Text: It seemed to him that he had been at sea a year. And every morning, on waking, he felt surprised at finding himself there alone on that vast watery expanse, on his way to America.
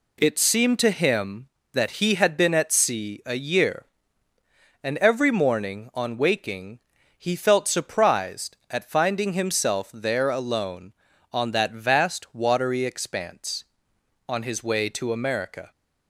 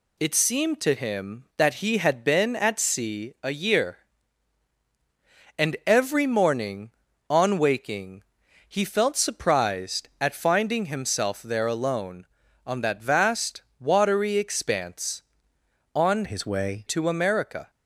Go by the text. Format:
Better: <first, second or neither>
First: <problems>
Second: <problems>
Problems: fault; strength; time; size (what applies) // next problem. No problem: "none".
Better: first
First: none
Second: pauses between "vast" and "watery"; slight; at 13.6 s; 0.18 s long // changes voice from "his" to "way"; from 16.2 to 16.8 s; 0.6 s long